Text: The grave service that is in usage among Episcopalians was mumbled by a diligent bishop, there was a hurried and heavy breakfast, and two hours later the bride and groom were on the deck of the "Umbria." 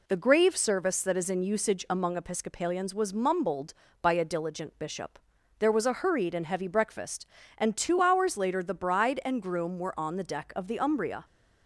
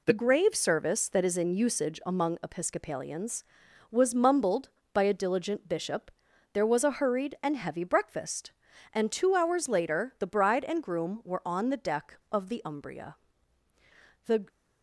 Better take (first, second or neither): first